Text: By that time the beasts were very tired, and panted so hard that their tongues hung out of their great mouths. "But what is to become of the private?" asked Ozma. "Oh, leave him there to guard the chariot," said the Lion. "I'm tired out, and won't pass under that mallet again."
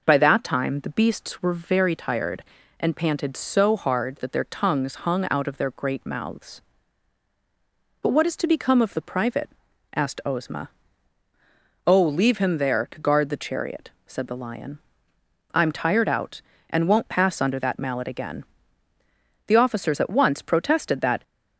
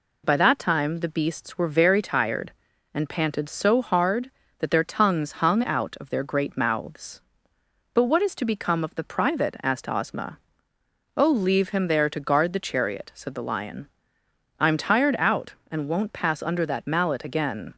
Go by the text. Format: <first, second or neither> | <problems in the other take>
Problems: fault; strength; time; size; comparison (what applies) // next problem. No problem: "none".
second | goes on to say "The officers at once protested that"; strong; from 19.4 s on; 1.7 s long